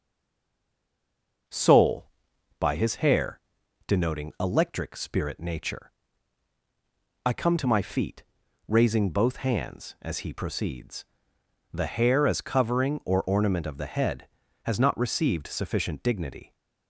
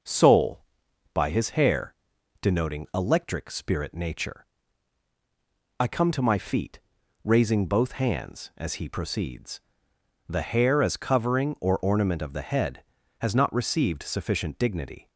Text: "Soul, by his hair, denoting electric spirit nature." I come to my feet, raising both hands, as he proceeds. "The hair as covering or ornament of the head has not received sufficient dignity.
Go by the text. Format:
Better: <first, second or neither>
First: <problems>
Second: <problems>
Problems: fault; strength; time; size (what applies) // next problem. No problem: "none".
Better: second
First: stays silent before the first word; noticeable; until 1.4 s; 1.4 s long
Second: none